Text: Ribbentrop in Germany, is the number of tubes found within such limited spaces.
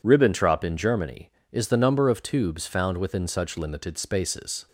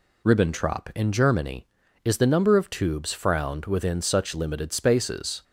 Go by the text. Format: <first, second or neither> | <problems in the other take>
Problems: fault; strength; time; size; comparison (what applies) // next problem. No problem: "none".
first | says "frowned" for "found"; at 3.1 s